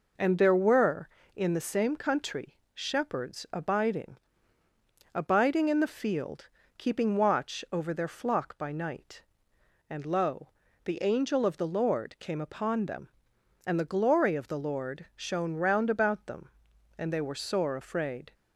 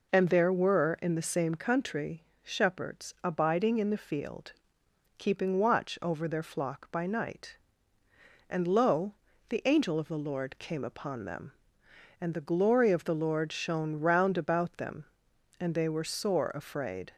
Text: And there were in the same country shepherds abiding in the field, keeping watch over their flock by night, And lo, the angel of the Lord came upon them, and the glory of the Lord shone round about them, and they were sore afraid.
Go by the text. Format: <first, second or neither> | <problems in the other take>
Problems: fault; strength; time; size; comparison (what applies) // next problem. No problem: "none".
second | pauses between "country" and "shepherds"; slight; at 2.5 s; 0.18 s long; slight in the second // says "abiding" twice; at 5.1 s